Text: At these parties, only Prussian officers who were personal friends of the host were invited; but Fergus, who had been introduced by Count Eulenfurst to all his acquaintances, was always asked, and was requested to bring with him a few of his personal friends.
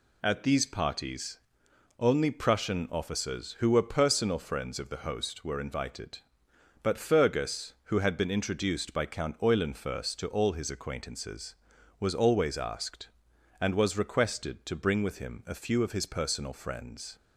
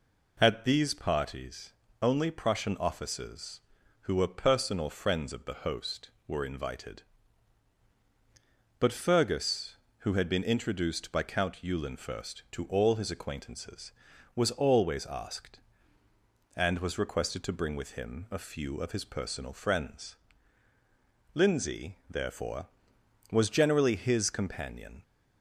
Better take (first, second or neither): first